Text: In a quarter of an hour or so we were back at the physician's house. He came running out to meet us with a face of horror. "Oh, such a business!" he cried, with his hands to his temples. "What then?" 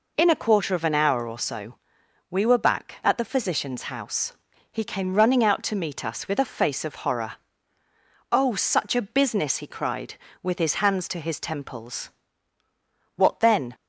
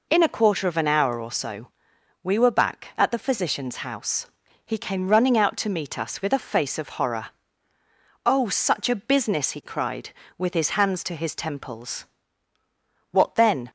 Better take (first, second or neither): neither